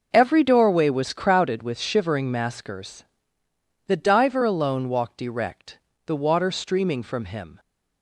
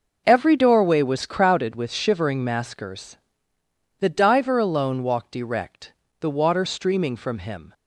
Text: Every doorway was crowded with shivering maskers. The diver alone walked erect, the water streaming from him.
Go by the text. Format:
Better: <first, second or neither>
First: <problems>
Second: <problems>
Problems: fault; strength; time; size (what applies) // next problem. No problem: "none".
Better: neither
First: none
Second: none